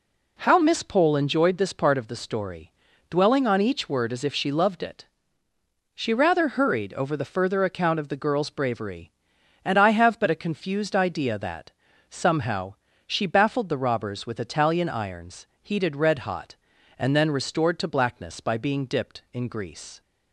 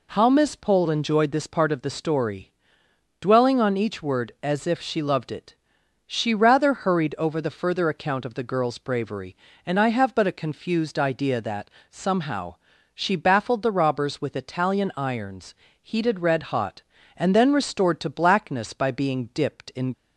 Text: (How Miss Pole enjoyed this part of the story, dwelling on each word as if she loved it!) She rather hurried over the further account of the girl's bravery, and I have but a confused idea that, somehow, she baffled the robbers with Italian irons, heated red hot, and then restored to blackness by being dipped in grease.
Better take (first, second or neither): first